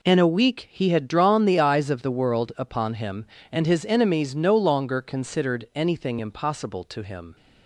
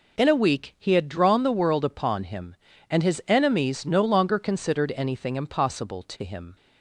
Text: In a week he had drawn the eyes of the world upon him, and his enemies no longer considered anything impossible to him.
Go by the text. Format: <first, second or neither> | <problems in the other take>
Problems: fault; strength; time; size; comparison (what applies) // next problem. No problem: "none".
first | skips "the eyes of"; at 1.4 s